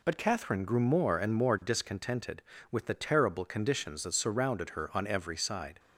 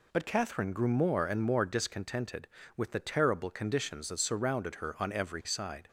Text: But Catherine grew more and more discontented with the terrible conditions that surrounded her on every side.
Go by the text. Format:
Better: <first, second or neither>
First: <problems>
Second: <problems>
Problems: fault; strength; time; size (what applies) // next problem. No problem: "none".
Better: neither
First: none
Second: none